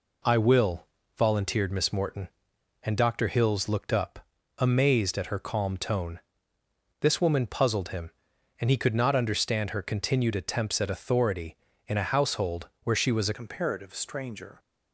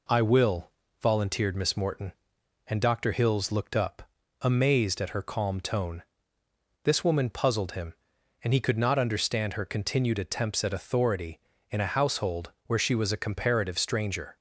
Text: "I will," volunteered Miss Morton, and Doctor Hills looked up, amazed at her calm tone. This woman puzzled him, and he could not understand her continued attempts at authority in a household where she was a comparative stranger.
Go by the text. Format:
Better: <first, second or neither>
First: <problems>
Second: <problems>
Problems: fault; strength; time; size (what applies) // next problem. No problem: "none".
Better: second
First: changes voice at "comparative"; from 13.3 s on; 1.2 s long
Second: none